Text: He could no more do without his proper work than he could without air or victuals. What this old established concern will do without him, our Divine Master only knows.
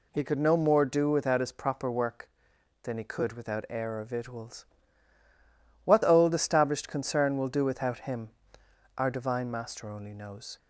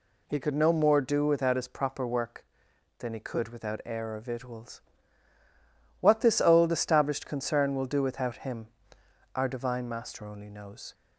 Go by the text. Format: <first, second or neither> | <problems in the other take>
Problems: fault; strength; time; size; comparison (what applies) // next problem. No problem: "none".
second | skips "this"; at 6.0 s